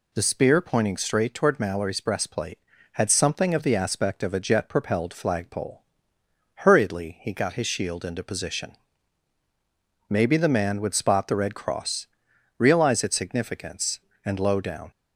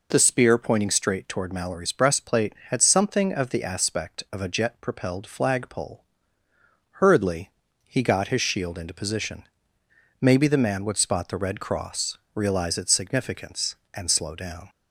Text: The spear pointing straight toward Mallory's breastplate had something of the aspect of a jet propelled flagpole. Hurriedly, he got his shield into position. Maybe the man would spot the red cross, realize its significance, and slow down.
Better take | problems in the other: second | says "low" for "slow"; at 14.3 s

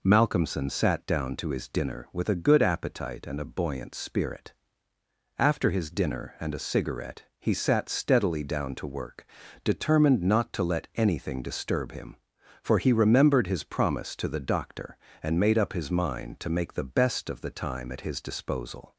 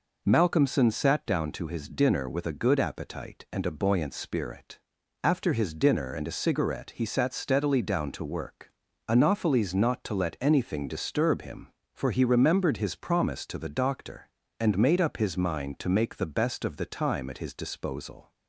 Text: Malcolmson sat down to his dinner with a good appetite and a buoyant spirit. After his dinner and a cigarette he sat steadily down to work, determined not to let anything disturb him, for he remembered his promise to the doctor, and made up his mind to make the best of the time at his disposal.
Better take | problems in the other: first | says "anopheles" for "determined"; at 9.0 s

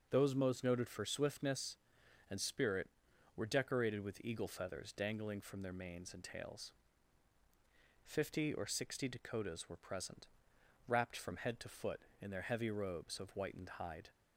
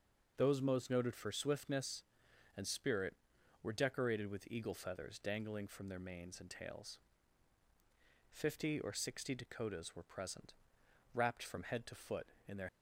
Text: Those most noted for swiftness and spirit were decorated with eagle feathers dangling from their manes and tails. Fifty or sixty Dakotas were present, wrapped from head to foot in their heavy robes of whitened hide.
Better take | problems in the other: first | stops before "heavy robes of whitened hide"; at 12.6 s

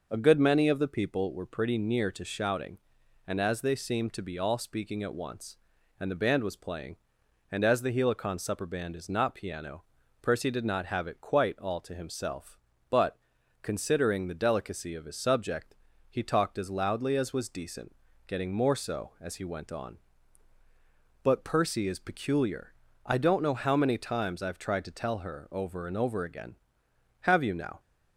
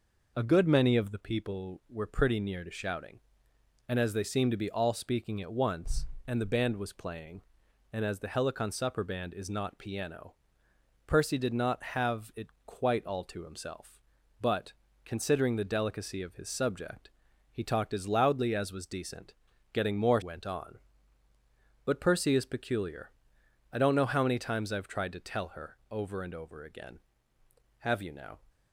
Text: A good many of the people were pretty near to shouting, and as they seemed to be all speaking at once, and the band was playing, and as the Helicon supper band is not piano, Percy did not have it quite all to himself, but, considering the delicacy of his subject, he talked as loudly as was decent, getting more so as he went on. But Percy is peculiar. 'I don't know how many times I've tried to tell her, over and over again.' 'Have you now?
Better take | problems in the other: first | pauses between "it" and "quite"; slight; at 12.4 s; 0.18 s long // skips "so as he"; at 20.2 s

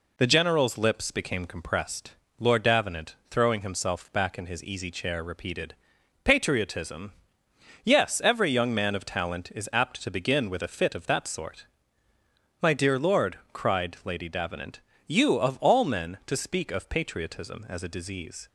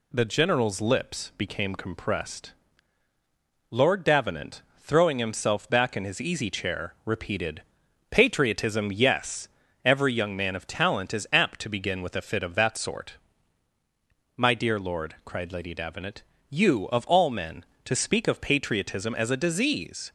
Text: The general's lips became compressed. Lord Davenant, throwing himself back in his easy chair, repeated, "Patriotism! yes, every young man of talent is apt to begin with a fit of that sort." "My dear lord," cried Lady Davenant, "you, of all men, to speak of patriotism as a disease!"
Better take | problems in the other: neither | none

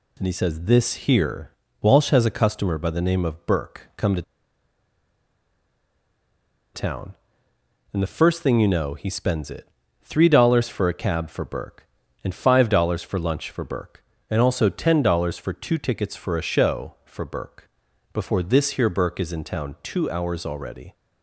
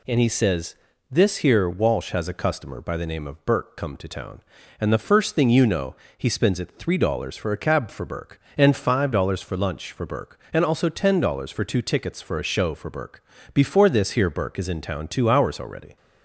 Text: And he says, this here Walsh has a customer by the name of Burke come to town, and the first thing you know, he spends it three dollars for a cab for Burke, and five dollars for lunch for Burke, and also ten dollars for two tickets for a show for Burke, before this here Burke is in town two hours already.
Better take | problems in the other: second | pauses between "here" and "Walsh"; slight; at 1.5 s; 0.28 s long // pauses between "to" and "town"; strong; at 4.2 s; 2.5 s long // pauses between "it" and "three"; slight; at 9.6 s; 0.34 s long

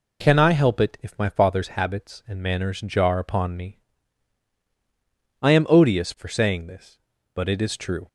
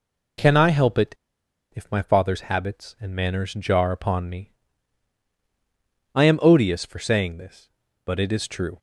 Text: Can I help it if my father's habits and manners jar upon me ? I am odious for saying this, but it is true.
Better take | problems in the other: first | pauses between "it" and "if"; noticeable; at 1.1 s; 0.57 s long

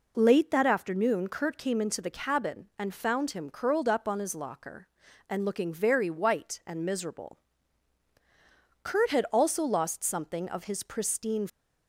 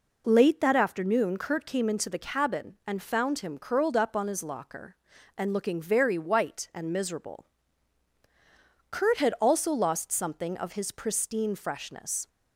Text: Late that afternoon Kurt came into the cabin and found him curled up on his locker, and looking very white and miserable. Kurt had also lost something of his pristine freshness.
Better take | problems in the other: second | stops before "freshness"; at 11.4 s

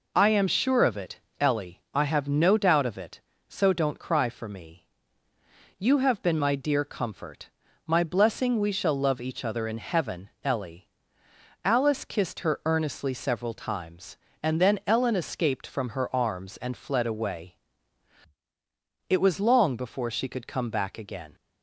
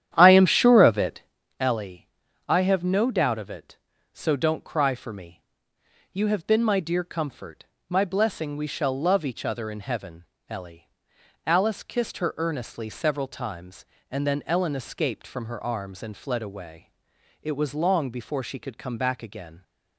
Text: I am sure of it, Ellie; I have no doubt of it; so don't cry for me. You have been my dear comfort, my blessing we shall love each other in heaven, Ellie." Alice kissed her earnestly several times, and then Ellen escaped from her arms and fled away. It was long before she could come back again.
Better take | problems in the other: first | starts louder than the rest; strong; until 1.5 s; 10.5 dB

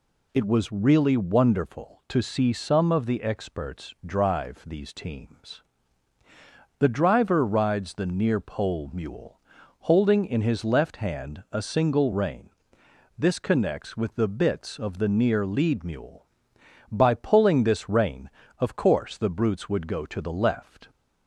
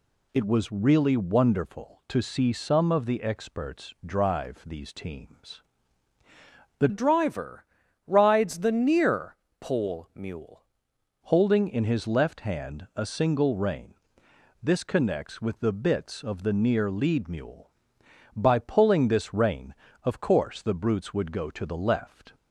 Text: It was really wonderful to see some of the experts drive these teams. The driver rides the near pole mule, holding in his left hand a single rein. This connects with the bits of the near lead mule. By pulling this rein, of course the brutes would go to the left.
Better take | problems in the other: first | changes voice from "driver" to "mule"; from 6.8 to 10.6 s; 3.8 s long // pauses between "driver" and "rides"; at 7.6 s; 0.42 s long // pauses between "near" and "pole"; slight; at 9.3 s; 0.24 s long

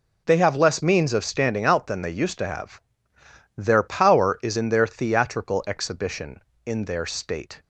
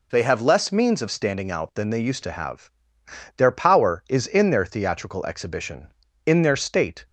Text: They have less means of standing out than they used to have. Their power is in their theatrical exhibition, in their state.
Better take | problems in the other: neither | none

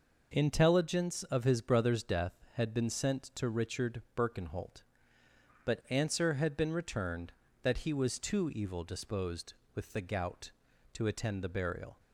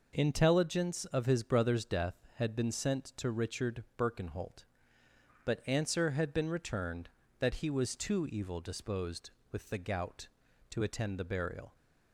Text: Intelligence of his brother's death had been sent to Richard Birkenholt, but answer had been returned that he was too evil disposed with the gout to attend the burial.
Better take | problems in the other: neither | pauses between "Richard" and "Birkenholt"; slight; the same in both

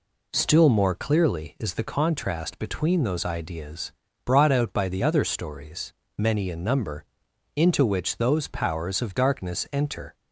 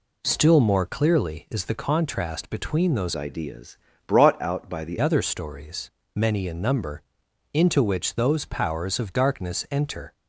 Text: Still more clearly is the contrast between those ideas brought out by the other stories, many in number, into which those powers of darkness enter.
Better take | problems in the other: first | changes voice from "ideas" to "the"; from 3.1 to 4.9 s; 1.8 s long // pauses between "ideas" and "brought"; slight; at 3.7 s; 0.28 s long; slight in the first

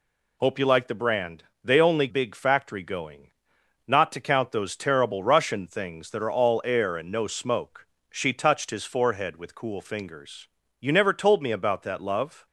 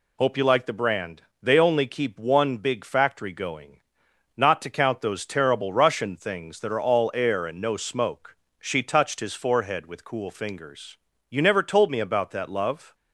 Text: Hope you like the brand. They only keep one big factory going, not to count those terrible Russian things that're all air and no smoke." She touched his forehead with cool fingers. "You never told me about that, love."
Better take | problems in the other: second | skips "keep one"; at 2.0 s

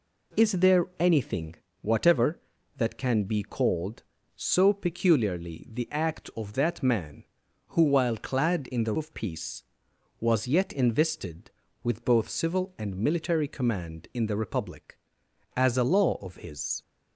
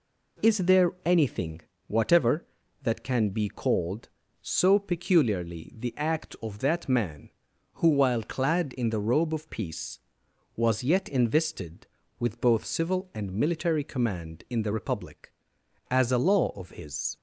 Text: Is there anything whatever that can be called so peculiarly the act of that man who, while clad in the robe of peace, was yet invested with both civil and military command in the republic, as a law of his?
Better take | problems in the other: second | pauses between "anything" and "whatever"; slight; at 1.5 s; 0.26 s long; slight in the second // skips "robe"; at 8.9 s

